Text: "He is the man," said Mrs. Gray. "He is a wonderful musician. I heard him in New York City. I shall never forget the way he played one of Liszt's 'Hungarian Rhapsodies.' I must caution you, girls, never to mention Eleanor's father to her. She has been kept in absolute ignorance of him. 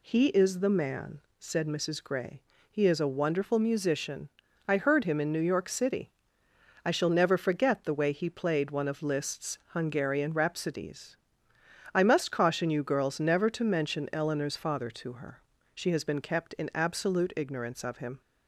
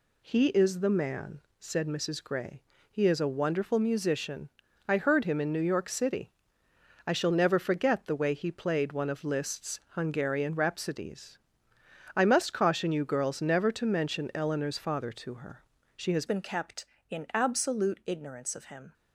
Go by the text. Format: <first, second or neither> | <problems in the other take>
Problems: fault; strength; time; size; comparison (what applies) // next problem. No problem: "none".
first | changes voice at "been"; from 16.2 s on; 2.7 s long